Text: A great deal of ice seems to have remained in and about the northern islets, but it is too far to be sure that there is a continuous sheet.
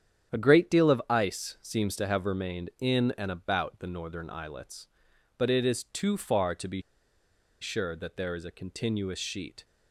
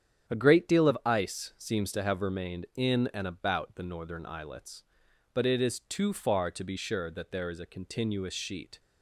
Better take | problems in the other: second | starts louder than the rest; strong; until 1.4 s; 9 dB; strong in the second // pauses between "be" and "sure"; noticeable; at 6.8 s; 0.79 s long

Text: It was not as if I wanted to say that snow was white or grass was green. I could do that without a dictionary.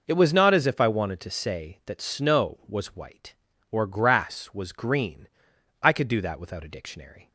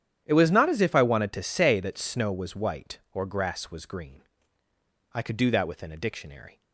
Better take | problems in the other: first | starts louder than the rest; strong; until 1.2 s; 10 dB // says "within" for "without"; at 5.6 s

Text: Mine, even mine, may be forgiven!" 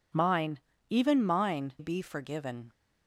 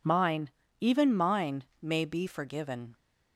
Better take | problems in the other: second | skips "may"; at 1.7 s

